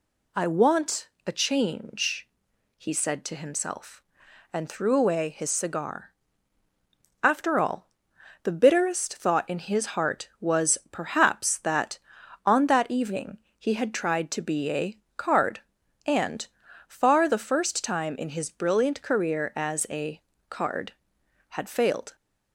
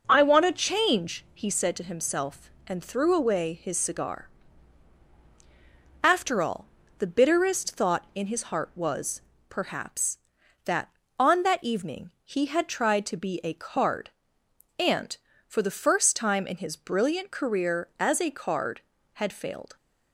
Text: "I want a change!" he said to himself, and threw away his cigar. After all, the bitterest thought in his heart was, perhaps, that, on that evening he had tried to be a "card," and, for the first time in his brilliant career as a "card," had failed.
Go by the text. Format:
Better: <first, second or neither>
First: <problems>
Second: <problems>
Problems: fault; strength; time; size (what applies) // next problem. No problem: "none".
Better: second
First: pauses between "want" and "a"; slight; at 1.0 s; 0.19 s long // pauses between "evening" and "he"; slight; at 13.3 s; 0.20 s long // pauses between "a" and "card"; slight; at 14.9 s; 0.20 s long // says "far" for "for"; at 16.8 s // pauses between "a" and "card"; slight; at 20.2 s; 0.28 s long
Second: none